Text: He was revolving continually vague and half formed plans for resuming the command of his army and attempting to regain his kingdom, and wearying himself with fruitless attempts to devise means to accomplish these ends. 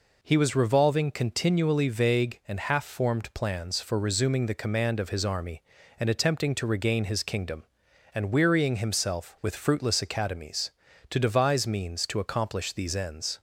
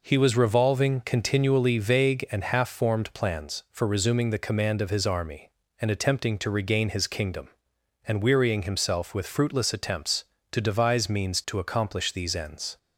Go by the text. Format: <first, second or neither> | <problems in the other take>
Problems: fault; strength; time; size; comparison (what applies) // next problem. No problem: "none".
second | says "academies" for "attempts"; at 10.0 s